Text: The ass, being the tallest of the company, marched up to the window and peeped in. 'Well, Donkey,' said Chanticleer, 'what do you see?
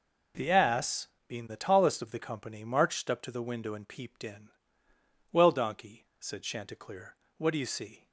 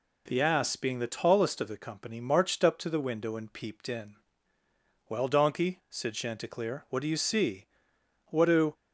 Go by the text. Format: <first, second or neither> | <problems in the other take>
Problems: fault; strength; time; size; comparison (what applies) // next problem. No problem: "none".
first | goes on to say "What do"; slight; from 8.3 s on; 0.42 s long